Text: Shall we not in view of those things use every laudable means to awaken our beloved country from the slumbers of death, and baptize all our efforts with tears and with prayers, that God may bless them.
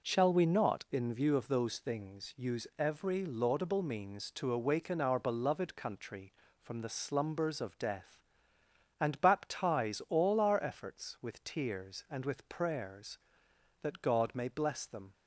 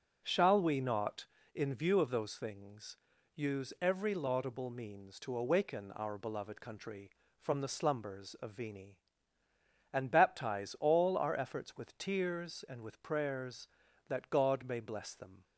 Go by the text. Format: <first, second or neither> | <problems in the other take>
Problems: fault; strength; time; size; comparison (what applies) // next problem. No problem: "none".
first | pauses between "things" and "use"; at 2.9 s; 0.40 s long // says "vini" for "death"; at 8.5 s